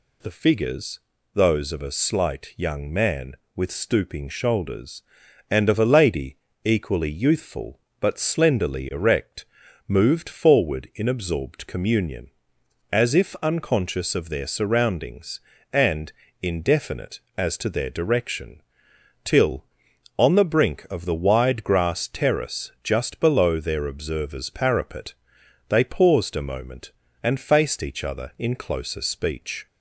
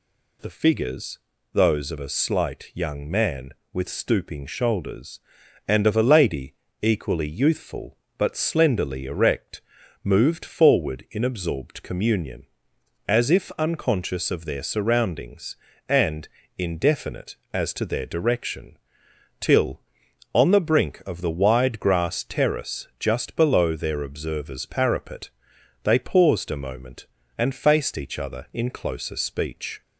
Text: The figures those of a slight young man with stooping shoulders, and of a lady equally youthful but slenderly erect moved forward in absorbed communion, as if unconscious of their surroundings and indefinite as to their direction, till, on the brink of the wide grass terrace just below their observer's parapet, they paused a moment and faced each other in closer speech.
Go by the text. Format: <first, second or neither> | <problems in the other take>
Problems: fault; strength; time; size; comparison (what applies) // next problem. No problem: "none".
neither | pauses between "figures" and "those"; slight; the same in both // pauses between "lady" and "equally"; slight; the same in both // pauses between "erect" and "moved"; the same in both // pauses between "and" and "indefinite"; slight; the same in both